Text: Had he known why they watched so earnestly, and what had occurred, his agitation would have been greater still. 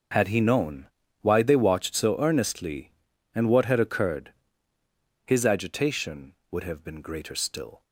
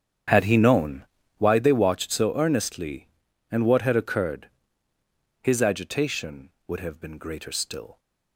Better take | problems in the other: first | starts louder than the rest; strong; until 1.5 s; 8.5 dB // pauses between "known" and "why"; slight; at 1.0 s; 0.34 s long; slight in the first

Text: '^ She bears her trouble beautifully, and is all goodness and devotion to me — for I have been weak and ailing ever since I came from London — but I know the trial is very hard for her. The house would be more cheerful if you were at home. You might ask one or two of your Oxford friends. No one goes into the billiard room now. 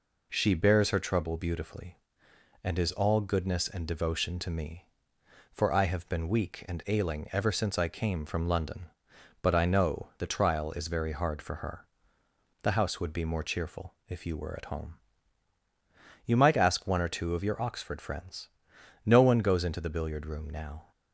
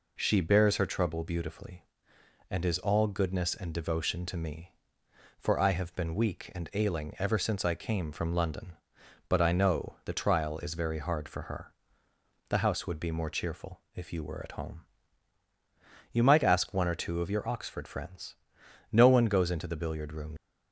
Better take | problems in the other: first | stops before "now"; at 20.3 s

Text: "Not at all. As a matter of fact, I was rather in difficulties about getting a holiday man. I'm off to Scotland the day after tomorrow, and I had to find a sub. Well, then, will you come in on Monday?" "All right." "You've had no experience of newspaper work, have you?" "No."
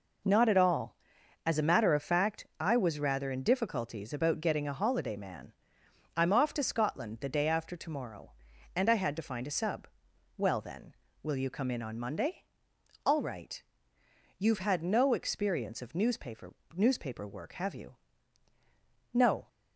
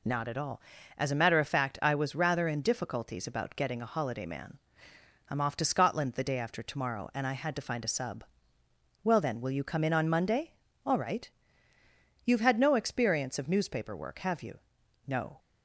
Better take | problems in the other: second | says "newspaper" twice; at 16.7 s

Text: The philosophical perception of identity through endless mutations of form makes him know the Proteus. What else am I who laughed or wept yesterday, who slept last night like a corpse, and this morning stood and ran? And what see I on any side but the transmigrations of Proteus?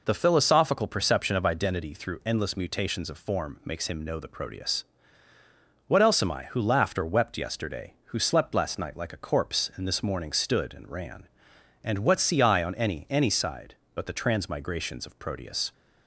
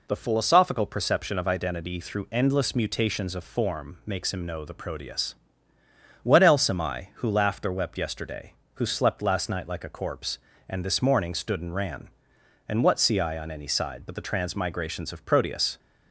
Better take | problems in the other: second | says "any" twice; at 13.1 s

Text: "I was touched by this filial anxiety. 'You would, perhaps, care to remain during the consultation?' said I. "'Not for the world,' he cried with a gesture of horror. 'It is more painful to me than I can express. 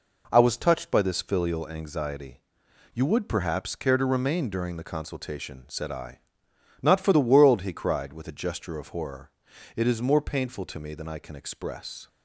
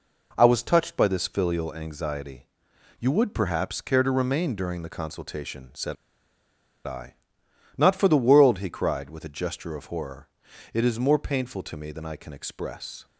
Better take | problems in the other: first | pauses between "said" and "I"; noticeable; at 5.9 s; 0.91 s long

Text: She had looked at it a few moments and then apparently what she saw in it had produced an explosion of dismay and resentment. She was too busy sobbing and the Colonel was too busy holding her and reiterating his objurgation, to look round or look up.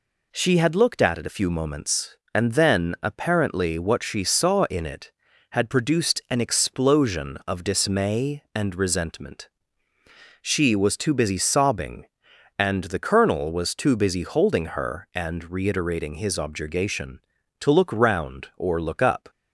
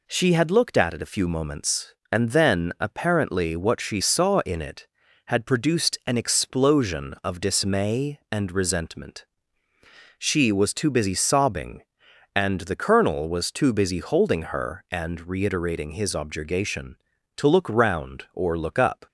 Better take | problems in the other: neither | none

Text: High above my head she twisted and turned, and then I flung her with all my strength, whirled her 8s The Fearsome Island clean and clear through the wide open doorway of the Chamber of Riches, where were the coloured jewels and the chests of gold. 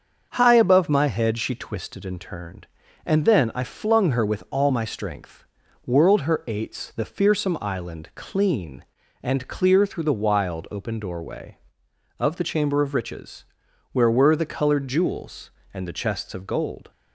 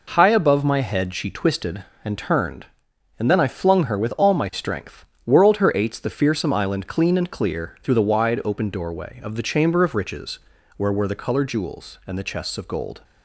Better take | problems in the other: second | starts louder than the rest; until 1.3 s; 6.5 dB // says "wild" for "wide"; at 10.1 s

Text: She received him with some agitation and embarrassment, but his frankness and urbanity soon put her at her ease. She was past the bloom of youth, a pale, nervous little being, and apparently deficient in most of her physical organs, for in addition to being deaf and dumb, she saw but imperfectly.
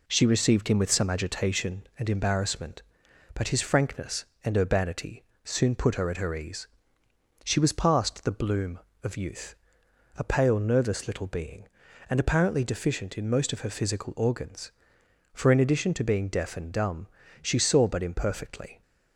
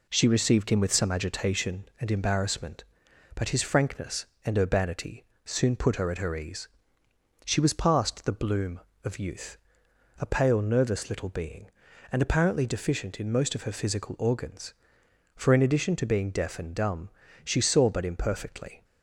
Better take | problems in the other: neither | pauses between "urbanity" and "soon"; slight; the same in both

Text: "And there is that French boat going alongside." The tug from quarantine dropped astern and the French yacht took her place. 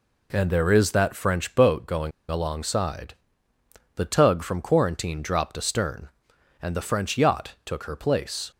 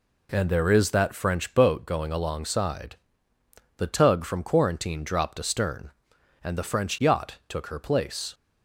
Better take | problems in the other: second | pauses between "going" and "alongside"; slight; at 2.1 s; 0.19 s long

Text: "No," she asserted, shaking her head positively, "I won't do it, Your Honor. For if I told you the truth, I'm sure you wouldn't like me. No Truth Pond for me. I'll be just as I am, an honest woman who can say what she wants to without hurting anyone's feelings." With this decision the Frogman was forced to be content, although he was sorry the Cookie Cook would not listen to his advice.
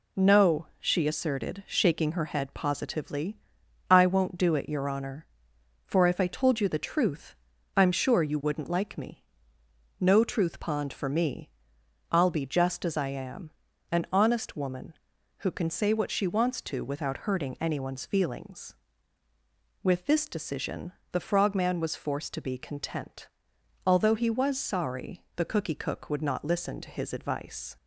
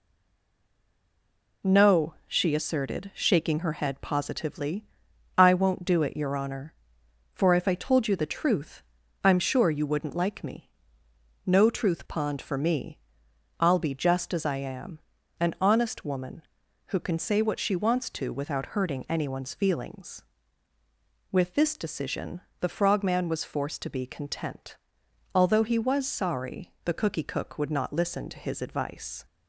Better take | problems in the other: first | stays silent before the first word; noticeable; until 1.6 s; 1.6 s long // pauses between "decision" and "the"; slight; at 22.4 s; 0.20 s long; slight in the first

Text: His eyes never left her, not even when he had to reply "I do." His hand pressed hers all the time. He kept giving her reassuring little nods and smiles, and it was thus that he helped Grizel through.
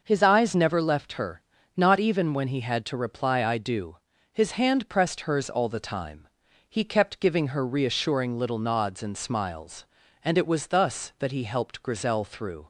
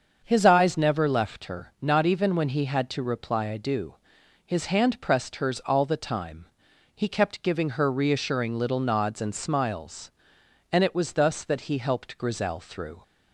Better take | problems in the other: neither | starts louder than the rest; the same in both

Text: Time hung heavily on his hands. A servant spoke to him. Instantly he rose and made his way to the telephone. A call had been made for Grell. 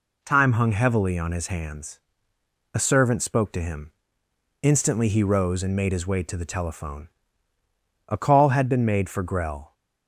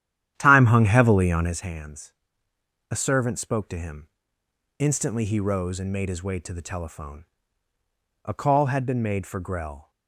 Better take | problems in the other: first | starts louder than the rest; strong; until 1.6 s; 11 dB

